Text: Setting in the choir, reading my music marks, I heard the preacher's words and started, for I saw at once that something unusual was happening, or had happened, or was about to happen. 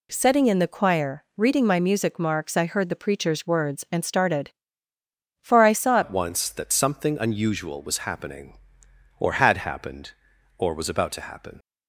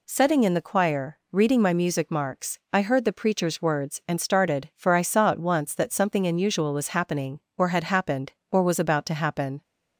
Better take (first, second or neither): second